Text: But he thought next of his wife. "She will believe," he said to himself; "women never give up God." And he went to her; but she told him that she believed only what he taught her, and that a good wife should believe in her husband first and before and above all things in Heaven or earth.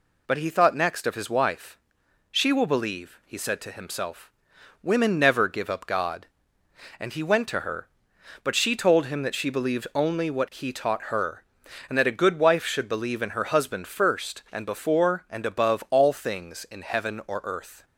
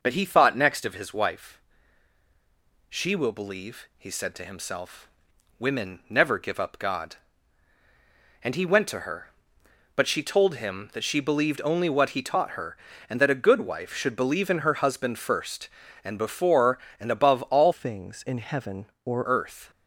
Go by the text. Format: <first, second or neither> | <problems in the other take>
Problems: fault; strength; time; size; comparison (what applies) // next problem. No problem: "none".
first | changes voice from "things" to "or"; from 17.7 to 19.2 s; 1.5 s long